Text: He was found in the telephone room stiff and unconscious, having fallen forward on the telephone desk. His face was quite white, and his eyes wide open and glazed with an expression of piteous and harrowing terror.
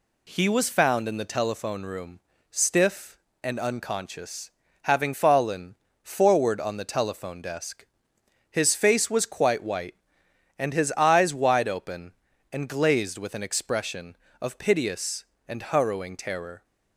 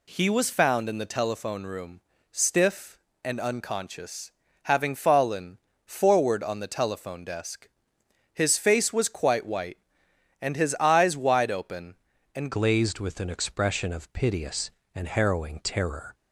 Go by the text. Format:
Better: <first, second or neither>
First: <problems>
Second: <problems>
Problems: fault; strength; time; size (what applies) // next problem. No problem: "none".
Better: first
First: pauses between "room" and "stiff"; slight; at 2.1 s; 0.30 s long // pauses between "fallen" and "forward"; slight; at 5.7 s; 0.26 s long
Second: pauses between "room" and "stiff"; slight; at 2.0 s; 0.30 s long // pauses between "fallen" and "forward"; slight; at 5.5 s; 0.26 s long // changes voice at "glazed"; from 12.5 s on; 3.6 s long